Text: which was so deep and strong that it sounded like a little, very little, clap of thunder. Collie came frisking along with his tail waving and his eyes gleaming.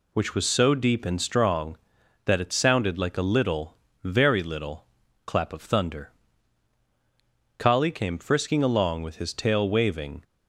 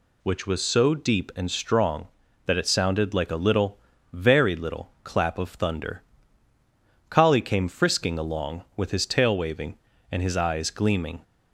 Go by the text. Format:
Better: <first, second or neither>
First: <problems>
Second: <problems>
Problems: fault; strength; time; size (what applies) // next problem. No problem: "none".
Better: second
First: stops before "and his eyes gleaming"; at 10.2 s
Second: none